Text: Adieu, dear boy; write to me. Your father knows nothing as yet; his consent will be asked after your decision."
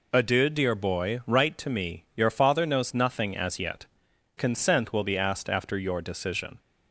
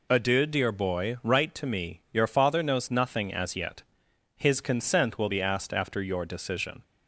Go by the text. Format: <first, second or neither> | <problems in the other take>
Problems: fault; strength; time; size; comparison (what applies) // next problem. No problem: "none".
second | skips "his"; at 4.1 s